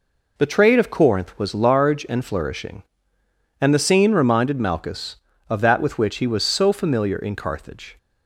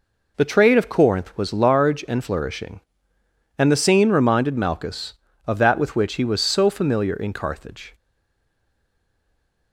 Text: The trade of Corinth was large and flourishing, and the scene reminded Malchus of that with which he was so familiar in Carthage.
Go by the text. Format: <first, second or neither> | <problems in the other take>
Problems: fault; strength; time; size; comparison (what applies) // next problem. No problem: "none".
first | stays silent after the last word; noticeable; from 7.9 s on; 1.8 s long